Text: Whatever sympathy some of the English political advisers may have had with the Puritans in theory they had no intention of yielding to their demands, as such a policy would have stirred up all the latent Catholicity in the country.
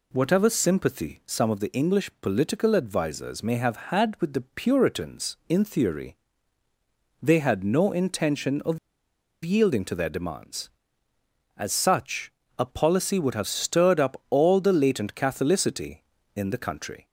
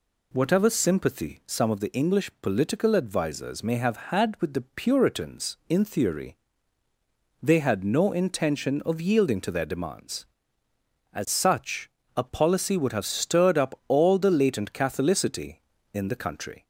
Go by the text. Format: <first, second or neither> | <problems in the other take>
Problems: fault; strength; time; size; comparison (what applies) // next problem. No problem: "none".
second | pauses between "theory" and "they"; at 6.1 s; 1.0 s long; also in the second // pauses between "of" and "yielding"; noticeable; at 8.7 s; 0.65 s long // pauses between "such" and "a"; slight; at 12.3 s; 0.28 s long; slight in the second